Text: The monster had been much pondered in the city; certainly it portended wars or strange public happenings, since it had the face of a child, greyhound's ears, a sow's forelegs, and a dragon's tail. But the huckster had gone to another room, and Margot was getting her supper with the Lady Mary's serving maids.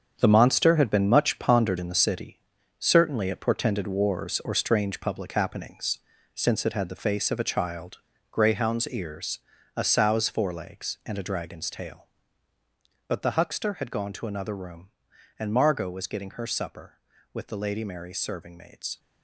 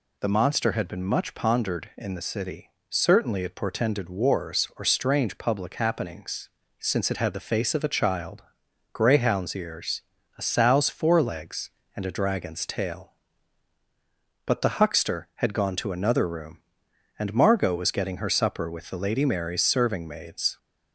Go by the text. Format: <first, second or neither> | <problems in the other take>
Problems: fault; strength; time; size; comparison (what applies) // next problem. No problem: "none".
second | gets quieter; strong; throughout; 10 dB